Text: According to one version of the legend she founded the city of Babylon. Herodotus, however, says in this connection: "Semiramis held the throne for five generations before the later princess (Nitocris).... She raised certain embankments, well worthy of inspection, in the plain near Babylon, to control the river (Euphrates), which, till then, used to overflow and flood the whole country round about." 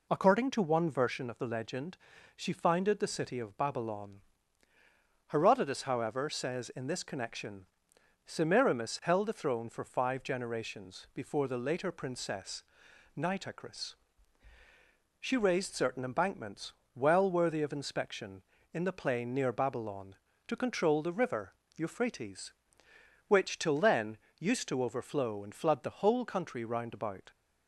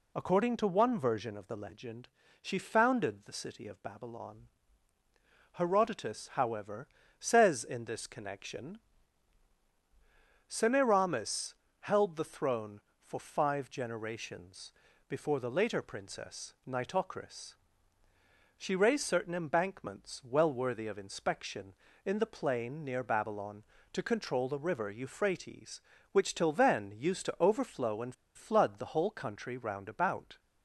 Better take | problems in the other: first | pauses between "legend" and "she"; slight; at 2.0 s; 0.32 s long; also in the first // pauses between "Semiramis" and "held"; slight; at 11.5 s; 0.26 s long // pauses between "generations" and "before"; slight; at 14.7 s; 0.36 s long // pauses between "and" and "flood"; slight; at 28.1 s; 0.22 s long

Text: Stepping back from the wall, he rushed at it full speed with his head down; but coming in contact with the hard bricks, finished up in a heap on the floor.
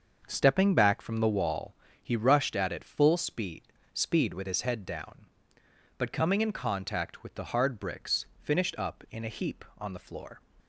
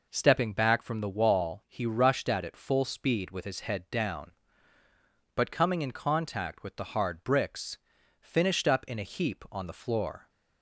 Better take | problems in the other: second | starts louder than the rest; until 1.2 s; 6.5 dB // says "speed" twice; at 3.9 s

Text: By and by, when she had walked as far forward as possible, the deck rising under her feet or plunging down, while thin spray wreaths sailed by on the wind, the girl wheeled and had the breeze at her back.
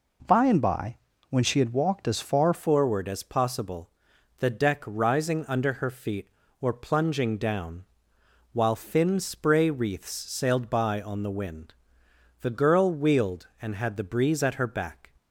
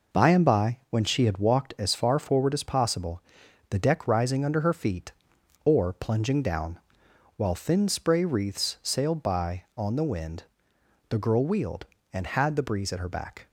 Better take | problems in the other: second | changes voice at "forward"; from 2.5 s on; 12.6 s long

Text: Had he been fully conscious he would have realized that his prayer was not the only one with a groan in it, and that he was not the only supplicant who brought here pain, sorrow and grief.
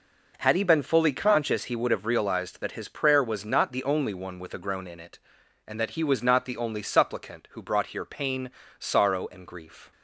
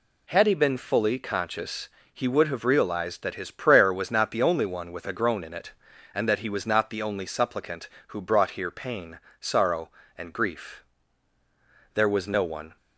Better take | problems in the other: first | pauses between "conscious" and "he"; slight; at 1.8 s; 0.24 s long // goes on to say "There was no one"; noticeable; from 11.9 s on; 0.82 s long

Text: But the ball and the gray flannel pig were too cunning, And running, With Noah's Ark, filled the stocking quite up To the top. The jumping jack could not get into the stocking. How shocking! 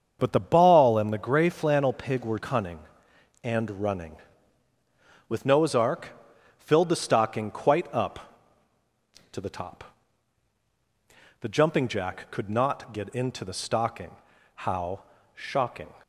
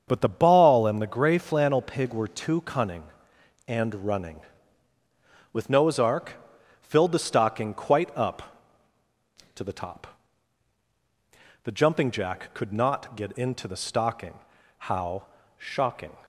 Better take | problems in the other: second | starts louder than the rest; until 1.2 s; 7 dB; also in the second // skips "too"; at 2.3 s // pauses between "How" and "shocking"; slight; at 15.0 s; 0.34 s long; slight in the second

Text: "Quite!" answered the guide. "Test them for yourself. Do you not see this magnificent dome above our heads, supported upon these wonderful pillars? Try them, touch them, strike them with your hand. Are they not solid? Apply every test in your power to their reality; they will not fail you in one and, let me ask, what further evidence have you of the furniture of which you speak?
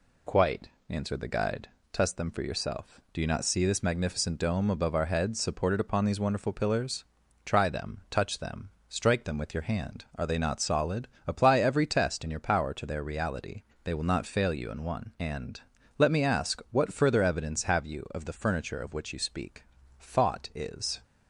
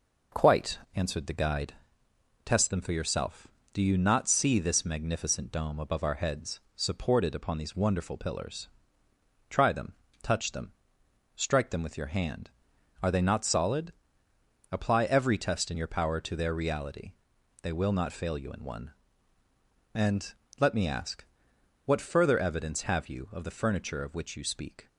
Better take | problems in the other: second | goes on to say "Thought is"; noticeable; from 19.9 s on; 1.0 s long

